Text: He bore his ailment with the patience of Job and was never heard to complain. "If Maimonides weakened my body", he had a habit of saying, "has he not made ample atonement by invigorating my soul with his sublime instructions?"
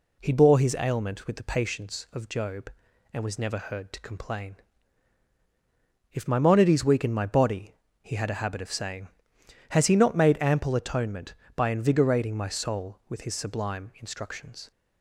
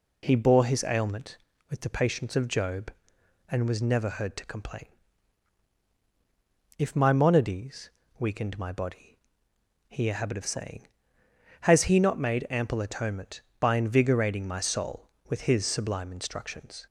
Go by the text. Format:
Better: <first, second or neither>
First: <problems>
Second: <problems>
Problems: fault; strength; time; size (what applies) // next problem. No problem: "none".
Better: first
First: none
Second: pauses between "Maimonides" and "weakened"; slight; at 7.8 s; 0.28 s long // skips "had"; at 10.0 s